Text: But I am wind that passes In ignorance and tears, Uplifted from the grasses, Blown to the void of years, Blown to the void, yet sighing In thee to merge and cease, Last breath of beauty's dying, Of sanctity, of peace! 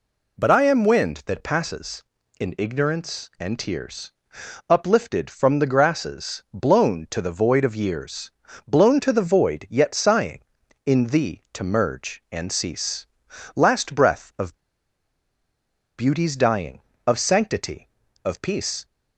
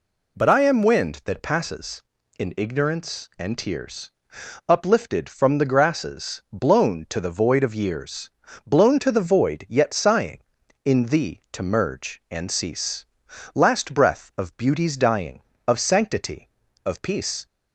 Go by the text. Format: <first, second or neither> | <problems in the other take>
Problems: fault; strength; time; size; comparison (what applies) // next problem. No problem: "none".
second | pauses between "of" and "beauty's"; strong; at 14.5 s; 1.4 s long